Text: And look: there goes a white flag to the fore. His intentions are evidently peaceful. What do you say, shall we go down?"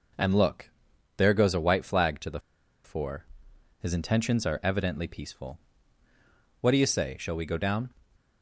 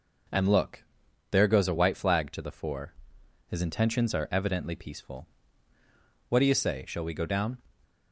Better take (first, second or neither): second